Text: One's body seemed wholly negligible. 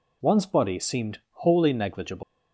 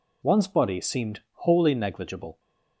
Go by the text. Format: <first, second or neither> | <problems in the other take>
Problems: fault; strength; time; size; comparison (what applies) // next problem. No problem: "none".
second | leaves "negligible" unfinished; at 2.2 s; 150 ms